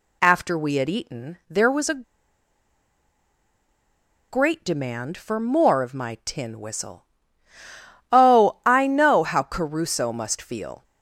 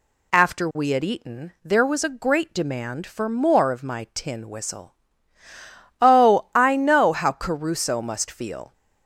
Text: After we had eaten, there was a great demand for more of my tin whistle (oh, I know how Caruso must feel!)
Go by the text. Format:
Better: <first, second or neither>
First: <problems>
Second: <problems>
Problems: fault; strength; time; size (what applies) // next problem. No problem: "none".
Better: second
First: pauses between "a" and "great"; strong; at 2.0 s; 2.2 s long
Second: none